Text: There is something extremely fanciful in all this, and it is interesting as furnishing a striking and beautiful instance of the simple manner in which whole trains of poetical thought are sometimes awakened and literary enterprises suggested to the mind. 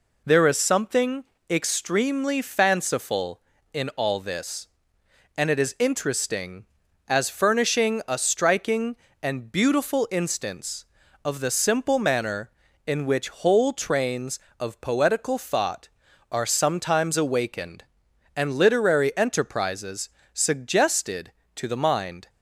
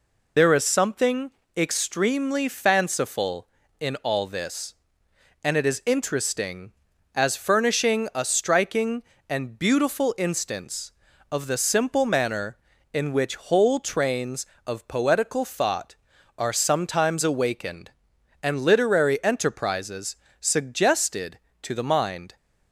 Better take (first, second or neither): first